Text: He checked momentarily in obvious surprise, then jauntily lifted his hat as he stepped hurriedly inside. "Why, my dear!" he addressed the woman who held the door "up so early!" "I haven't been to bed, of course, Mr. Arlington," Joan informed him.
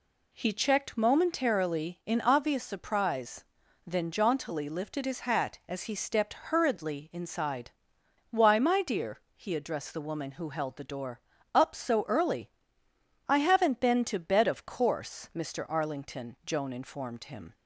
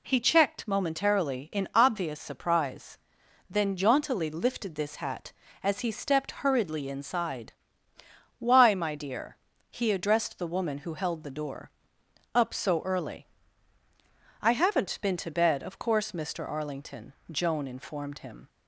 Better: first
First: pauses between "door" and "up"; slight; at 11.1 s; 0.34 s long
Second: says "this" for "his"; at 4.7 s // pauses between "door" and "up"; noticeable; at 11.7 s; 0.64 s long

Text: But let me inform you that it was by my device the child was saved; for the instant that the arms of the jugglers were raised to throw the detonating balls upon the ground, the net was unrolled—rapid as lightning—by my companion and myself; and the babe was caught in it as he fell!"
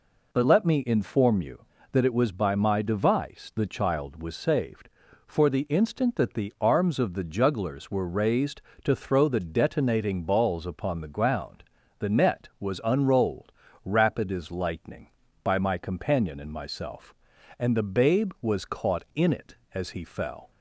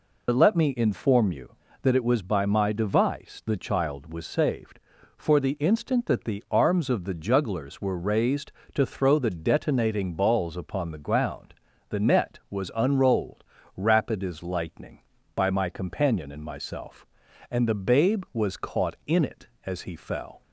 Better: first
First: none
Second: loses the start of "But"; at 0.2 s; 55 ms

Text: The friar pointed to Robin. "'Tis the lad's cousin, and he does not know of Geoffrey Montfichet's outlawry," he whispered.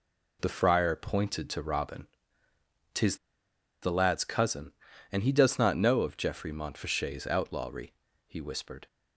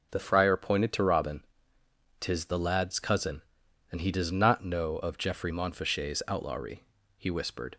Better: second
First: pauses between "Tis" and "the"; noticeable; at 3.1 s; 0.65 s long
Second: none

